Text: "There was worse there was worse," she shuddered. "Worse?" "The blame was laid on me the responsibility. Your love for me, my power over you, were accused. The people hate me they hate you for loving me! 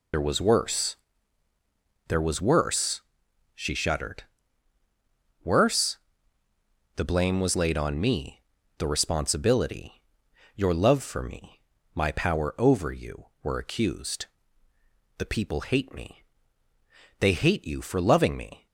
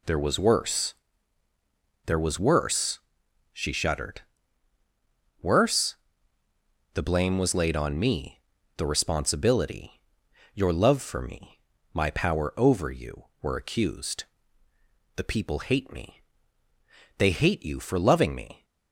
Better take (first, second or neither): second